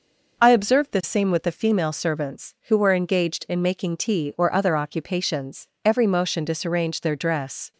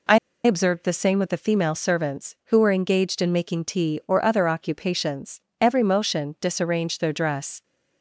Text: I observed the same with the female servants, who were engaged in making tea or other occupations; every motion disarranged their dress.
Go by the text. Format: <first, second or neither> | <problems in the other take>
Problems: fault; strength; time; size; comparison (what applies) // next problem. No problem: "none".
first | pauses between "I" and "observed"; slight; at 0.1 s; 0.26 s long